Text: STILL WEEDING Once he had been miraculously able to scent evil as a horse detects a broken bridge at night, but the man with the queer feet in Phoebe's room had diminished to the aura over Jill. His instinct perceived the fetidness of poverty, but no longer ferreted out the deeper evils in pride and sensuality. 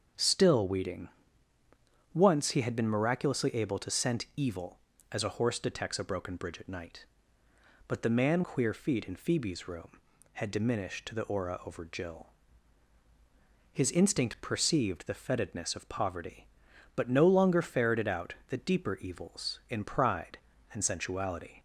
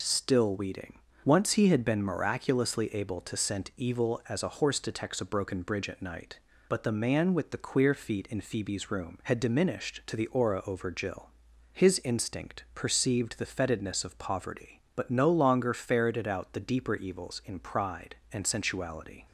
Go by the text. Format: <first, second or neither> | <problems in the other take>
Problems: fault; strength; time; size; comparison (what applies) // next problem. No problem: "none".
second | starts louder than the rest; until 2.2 s; 7 dB // pauses between "WEEDING" and "Once"; at 1.0 s; 1.0 s long; slight in the second // skips "with the"; at 8.4 s